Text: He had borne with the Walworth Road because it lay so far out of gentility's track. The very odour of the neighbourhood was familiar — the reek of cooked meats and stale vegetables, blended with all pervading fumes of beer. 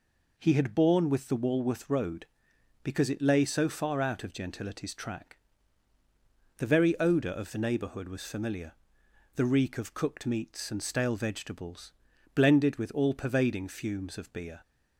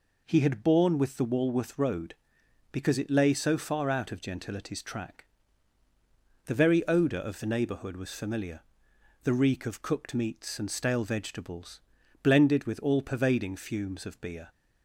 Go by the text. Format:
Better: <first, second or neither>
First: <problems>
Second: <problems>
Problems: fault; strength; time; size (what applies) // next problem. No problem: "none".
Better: neither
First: none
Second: none